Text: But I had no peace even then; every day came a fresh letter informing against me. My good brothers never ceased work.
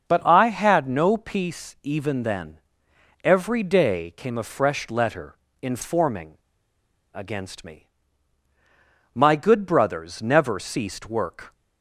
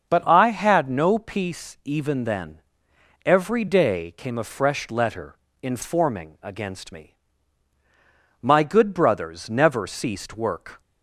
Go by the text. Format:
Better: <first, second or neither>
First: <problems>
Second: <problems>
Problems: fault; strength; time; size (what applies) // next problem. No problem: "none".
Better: second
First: starts louder than the rest; until 1.1 s; 7 dB // pauses between "letter" and "informing"; slight; at 5.3 s; 0.26 s long // pauses between "informing" and "against"; noticeable; at 6.3 s; 0.76 s long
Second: starts louder than the rest; until 1.1 s; 7 dB // pauses between "letter" and "informing"; slight; at 5.3 s; 0.26 s long